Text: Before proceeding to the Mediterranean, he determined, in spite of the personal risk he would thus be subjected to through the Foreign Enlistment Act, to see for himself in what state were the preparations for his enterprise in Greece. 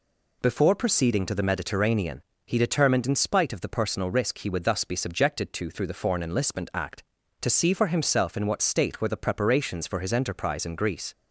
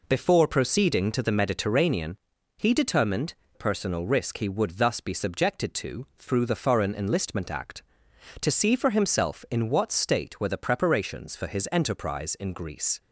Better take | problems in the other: first | skips "in spite of the"; at 3.4 s

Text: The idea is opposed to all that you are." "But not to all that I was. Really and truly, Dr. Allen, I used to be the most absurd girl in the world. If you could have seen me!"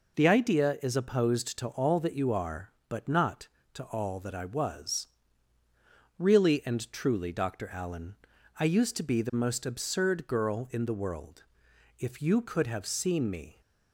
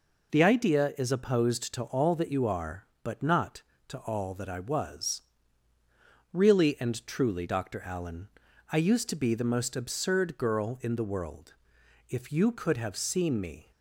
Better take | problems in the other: neither | none

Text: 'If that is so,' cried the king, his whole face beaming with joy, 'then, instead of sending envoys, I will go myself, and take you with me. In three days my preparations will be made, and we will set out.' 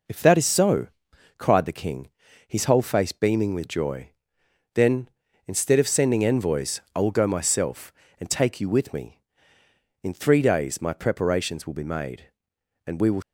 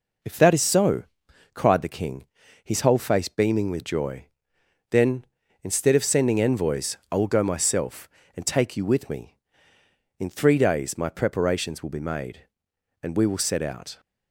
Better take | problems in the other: second | stops before "set out"; at 13.2 s

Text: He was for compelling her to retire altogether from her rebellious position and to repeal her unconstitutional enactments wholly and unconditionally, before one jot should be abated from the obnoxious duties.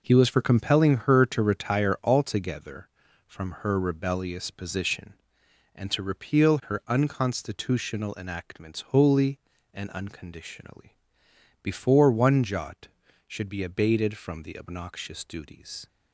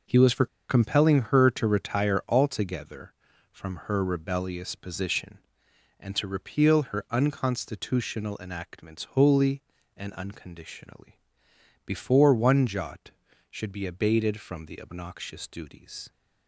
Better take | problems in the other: first | starts louder than the rest; until 1.4 s; 6 dB // pauses between "for" and "compelling"; slight; at 0.4 s; 0.23 s long

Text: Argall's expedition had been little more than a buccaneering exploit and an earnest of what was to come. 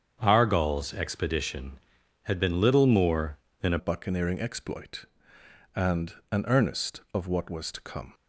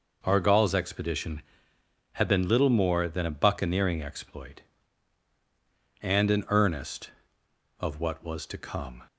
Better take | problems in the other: second | starts louder than the rest; strong; until 1.2 s; 7.5 dB // changes voice at "buccaneering"; from 3.7 s on; 4.4 s long // pauses between "and" and "an"; slight; at 6.1 s; 0.16 s long

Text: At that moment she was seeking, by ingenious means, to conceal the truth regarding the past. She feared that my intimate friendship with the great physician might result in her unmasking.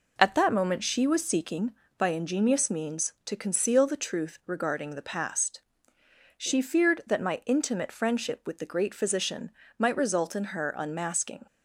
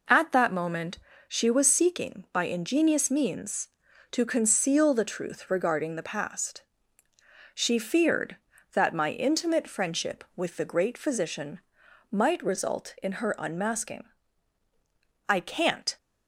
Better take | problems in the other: first | pauses between "moment" and "she"; slight; at 0.9 s; 0.30 s long // pauses between "physician" and "might"; noticeable; at 11.6 s; 0.50 s long; slight in the first // goes on to say "I can't"; noticeable; from 15.2 s on; 0.68 s long

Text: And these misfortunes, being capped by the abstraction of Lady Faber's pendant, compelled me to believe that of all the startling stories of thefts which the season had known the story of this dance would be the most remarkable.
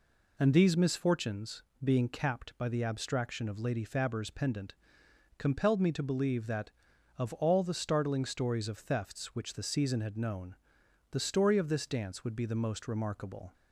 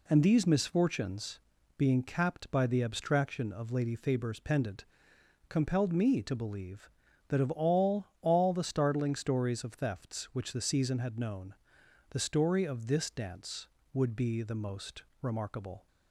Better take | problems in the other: first | says "all" twice; at 8.2 s // pauses between "known" and "the"; noticeable; at 11.5 s; 0.56 s long; noticeable in the first // pauses between "most" and "remarkable"; slight; at 15.0 s; 0.18 s long

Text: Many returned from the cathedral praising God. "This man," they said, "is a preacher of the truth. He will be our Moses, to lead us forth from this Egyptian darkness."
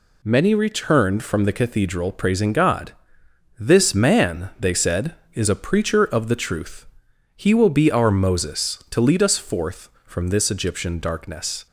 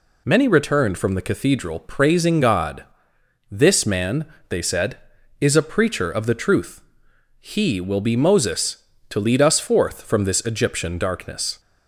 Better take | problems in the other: first | skips "our"; at 8.1 s

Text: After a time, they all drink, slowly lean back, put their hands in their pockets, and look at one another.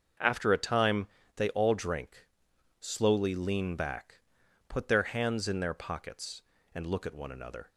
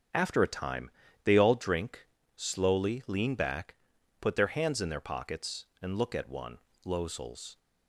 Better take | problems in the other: first | starts louder than the rest; strong; until 1.4 s; 7.5 dB; also in the first // says "losels" for "another"; at 6.8 s

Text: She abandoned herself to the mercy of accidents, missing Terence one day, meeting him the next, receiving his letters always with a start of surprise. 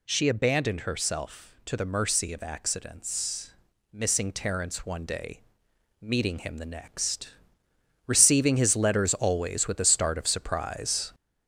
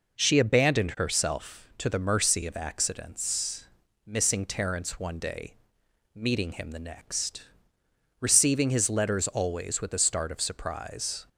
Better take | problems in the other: second | gets louder; noticeable; throughout; 4.5 dB

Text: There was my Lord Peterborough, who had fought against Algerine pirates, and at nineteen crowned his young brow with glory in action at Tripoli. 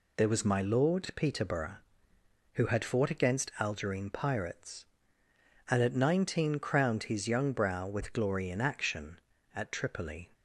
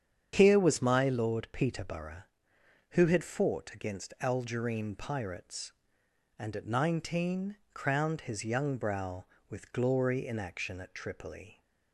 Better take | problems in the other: first | starts louder than the rest; strong; until 1.3 s; 8 dB // says "Here" for "There"; at 0.3 s // pauses between "nineteen" and "crowned"; slight; at 7.5 s; 0.18 s long

